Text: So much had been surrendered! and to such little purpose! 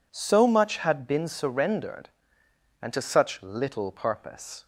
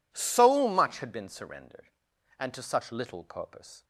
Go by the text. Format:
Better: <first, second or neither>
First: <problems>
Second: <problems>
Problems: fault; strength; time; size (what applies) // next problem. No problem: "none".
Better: neither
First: none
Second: none